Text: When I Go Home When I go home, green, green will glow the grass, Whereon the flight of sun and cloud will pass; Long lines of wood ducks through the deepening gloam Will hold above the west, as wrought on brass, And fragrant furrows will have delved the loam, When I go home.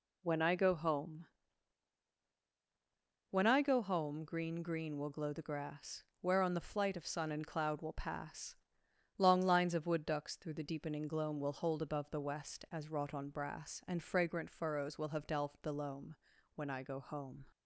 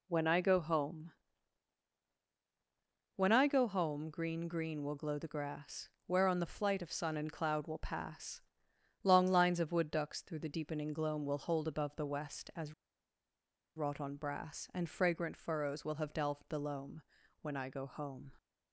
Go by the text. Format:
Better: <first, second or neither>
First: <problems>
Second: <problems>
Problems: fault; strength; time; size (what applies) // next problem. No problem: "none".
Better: first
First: pauses between "Home" and "When"; strong; at 1.2 s; 2.0 s long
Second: pauses between "Home" and "When"; strong; at 1.1 s; 2.0 s long // pauses between "as" and "wrought"; at 12.7 s; 1.0 s long